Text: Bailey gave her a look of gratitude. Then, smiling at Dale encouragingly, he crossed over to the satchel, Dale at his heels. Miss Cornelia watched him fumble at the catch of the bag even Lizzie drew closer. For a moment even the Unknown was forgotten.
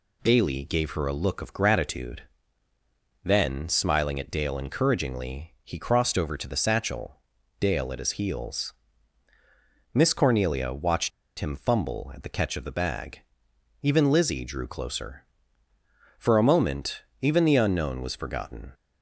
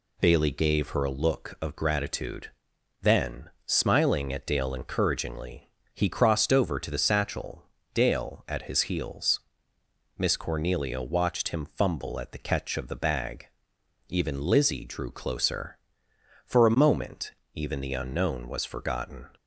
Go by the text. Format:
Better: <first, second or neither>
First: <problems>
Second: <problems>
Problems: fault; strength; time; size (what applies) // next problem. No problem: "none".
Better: second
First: pauses between "watched" and "him"; slight; at 11.1 s; 0.29 s long // pauses between "bag" and "even"; noticeable; at 13.1 s; 0.62 s long // pauses between "moment" and "even"; slight; at 17.0 s; 0.18 s long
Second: pauses between "bag" and "even"; noticeable; at 13.4 s; 0.62 s long // pauses between "moment" and "even"; slight; at 17.3 s; 0.20 s long